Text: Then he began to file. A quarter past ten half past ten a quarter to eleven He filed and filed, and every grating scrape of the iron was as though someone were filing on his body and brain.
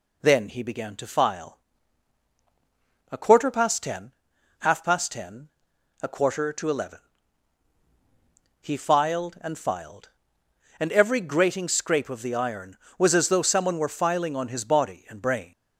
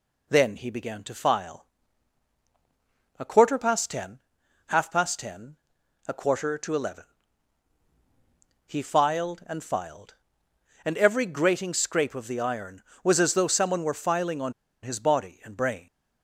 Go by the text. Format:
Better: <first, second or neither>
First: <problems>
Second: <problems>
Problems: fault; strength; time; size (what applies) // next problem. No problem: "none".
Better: first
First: pauses between "ten" and "half"; noticeable; at 4.1 s; 0.48 s long // pauses between "ten" and "a"; noticeable; at 5.4 s; 0.52 s long // pauses between "eleven" and "He"; strong; at 6.9 s; 1.6 s long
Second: pauses between "ten" and "half"; noticeable; at 4.1 s; 0.48 s long // pauses between "ten" and "a"; noticeable; at 5.5 s; 0.50 s long // pauses between "eleven" and "He"; strong; at 7.0 s; 1.6 s long // pauses between "on" and "his"; slight; at 14.5 s; 0.29 s long